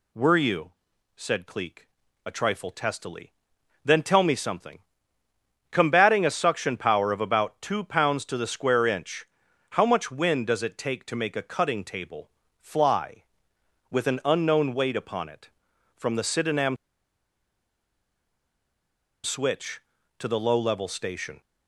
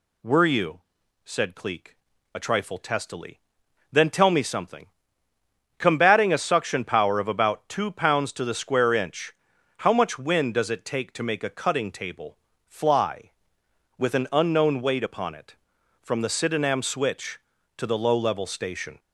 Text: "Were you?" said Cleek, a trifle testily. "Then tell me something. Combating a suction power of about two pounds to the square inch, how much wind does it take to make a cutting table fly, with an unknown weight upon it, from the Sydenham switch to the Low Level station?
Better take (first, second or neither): second